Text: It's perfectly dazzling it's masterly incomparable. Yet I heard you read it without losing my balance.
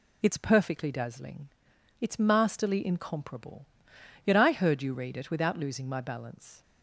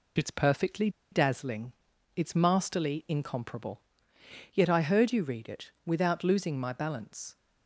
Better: first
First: pauses between "dazzling" and "it's"; noticeable; at 1.4 s; 0.52 s long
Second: pauses between "perfectly" and "dazzling"; slight; at 0.8 s; 0.22 s long // pauses between "dazzling" and "it's"; at 1.7 s; 0.42 s long

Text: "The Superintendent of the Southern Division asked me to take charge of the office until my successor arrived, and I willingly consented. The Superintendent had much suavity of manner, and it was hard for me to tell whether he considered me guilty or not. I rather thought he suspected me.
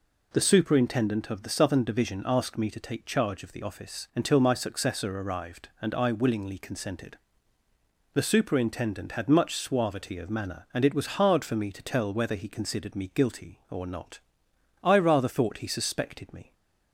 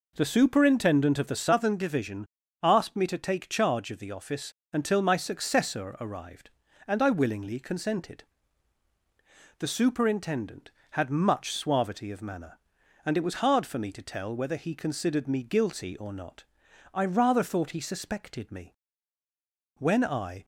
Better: first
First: none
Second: pauses between "Division" and "asked"; slight; at 2.2 s; 0.34 s long // pauses between "office" and "until"; slight; at 4.5 s; 0.18 s long // goes on to say "When I"; noticeable; from 19.7 s on; 0.66 s long

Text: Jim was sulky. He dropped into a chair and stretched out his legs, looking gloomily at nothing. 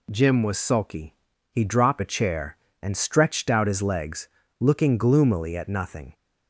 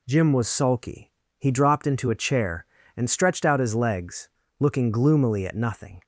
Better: second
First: skips "into"; at 2.0 s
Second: none

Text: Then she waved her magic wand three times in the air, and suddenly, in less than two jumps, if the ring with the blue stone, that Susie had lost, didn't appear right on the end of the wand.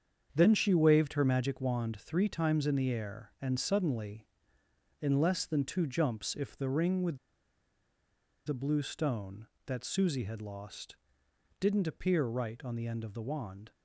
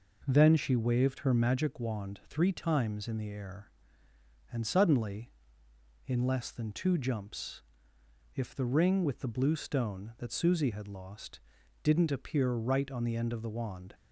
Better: second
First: starts louder than the rest; strong; until 1.3 s; 7.5 dB // pauses between "with" and "the"; strong; at 7.1 s; 1.2 s long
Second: none

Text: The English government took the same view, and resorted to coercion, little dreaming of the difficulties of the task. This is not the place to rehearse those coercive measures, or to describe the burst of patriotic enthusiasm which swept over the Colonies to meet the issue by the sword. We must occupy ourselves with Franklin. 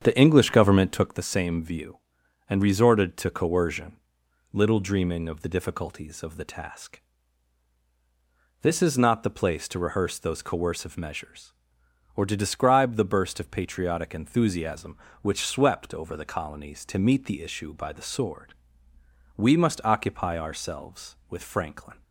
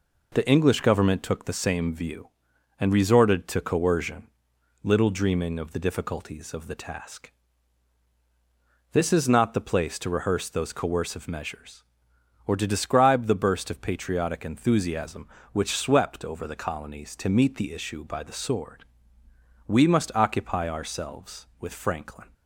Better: second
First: starts louder than the rest; strong; until 1.2 s; 8 dB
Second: none

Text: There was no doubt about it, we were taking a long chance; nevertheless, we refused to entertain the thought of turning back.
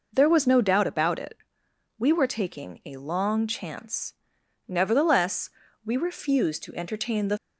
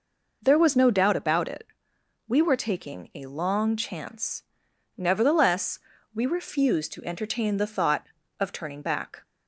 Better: second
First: stops before "thought of turning back"; at 7.3 s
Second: none

